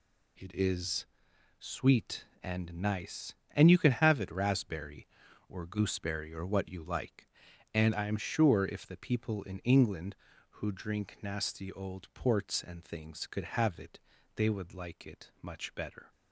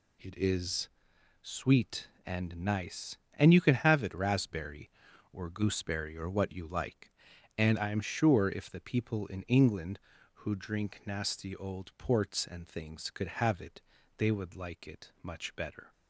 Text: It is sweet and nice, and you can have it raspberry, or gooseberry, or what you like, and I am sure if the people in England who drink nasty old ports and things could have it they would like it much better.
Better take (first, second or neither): neither